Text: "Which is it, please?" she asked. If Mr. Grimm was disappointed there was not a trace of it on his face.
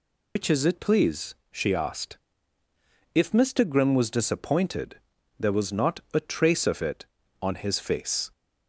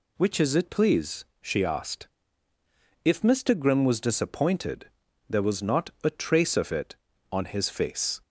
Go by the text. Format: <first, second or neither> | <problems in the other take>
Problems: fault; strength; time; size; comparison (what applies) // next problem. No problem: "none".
second | loses the start of "Which"; at 0.3 s; 80 ms // pauses between "disappointed" and "there"; at 4.9 s; 0.40 s long; also in the second